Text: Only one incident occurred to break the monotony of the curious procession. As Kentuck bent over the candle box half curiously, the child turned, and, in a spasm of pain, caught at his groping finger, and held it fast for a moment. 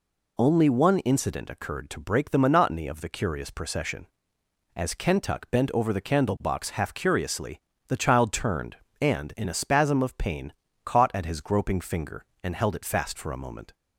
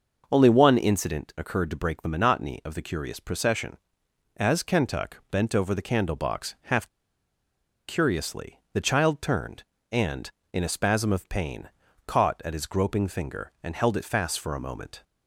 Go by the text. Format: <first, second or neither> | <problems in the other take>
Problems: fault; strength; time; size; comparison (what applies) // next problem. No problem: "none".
first | pauses between "half" and "curiously"; at 6.8 s; 1.0 s long